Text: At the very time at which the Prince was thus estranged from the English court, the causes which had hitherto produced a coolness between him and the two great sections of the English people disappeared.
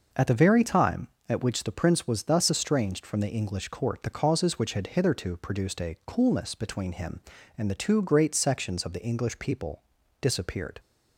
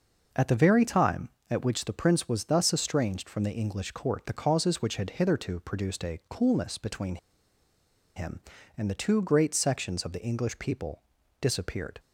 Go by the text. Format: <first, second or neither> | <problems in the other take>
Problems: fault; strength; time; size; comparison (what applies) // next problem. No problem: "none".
first | pauses between "between" and "him"; at 7.1 s; 0.99 s long // pauses between "people" and "disappeared"; at 11.0 s; 0.40 s long; also in the first